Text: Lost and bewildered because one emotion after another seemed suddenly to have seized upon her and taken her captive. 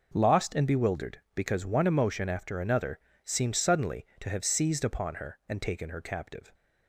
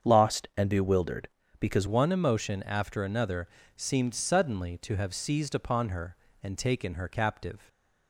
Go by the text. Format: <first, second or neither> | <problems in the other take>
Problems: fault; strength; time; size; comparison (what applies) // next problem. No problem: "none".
first | starts louder than the rest; strong; until 1.1 s; 7.5 dB // changes voice at "one"; from 1.8 s on; 5.8 s long // pauses between "another" and "seemed"; slight; at 3.4 s; 0.28 s long; slight in the first